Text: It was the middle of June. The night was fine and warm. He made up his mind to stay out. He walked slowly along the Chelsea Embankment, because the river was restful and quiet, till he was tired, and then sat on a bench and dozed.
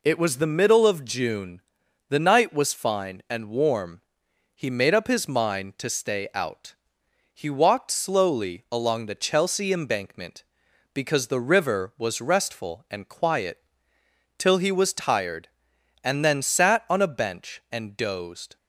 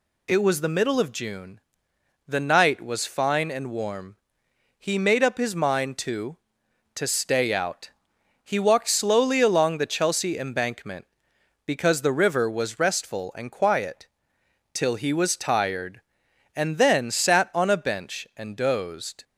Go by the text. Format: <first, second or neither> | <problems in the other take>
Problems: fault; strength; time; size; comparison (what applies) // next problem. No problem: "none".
first | says "to" twice; at 6.9 s